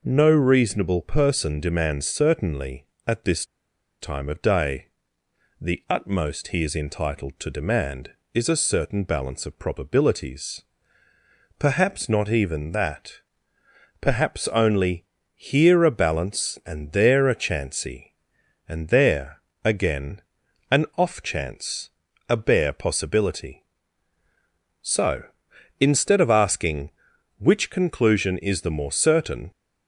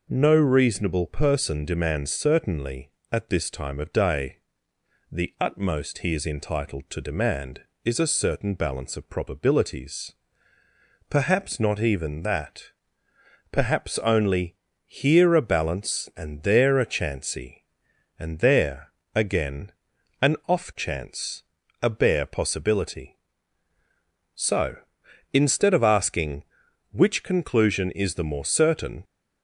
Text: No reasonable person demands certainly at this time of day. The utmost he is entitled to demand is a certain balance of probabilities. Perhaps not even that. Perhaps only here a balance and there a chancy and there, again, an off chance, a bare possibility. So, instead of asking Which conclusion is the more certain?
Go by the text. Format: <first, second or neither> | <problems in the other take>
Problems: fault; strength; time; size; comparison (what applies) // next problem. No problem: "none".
second | pauses between "this" and "time"; noticeable; at 3.4 s; 0.56 s long // pauses between "only" and "here"; slight; at 15.0 s; 0.30 s long; slight in the second